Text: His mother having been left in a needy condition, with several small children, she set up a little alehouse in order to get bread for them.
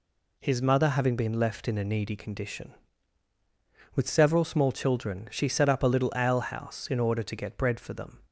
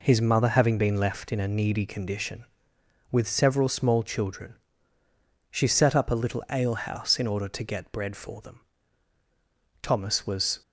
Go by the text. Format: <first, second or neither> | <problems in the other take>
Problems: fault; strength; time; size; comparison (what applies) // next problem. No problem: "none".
first | goes on to say "Thomas was"; noticeable; from 9.8 s on; 0.78 s long